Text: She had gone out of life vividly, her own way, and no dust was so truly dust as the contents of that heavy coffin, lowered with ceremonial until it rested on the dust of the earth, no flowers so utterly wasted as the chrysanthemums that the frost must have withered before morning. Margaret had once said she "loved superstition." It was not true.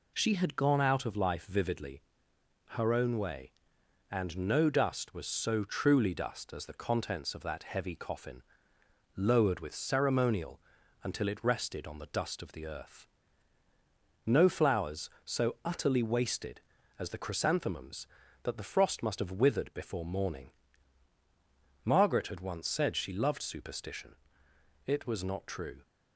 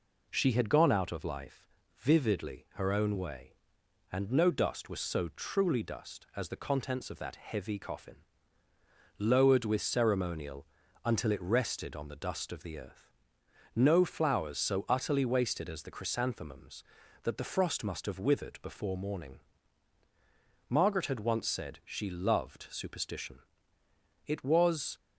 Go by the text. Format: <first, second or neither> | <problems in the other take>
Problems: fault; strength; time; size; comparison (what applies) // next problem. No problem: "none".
first | pauses between "life" and "vividly"; slight; at 1.6 s; 0.30 s long // pauses between "ceremonial" and "until"; at 10.6 s; 0.38 s long; also in the first // stops before "not true"; at 24.9 s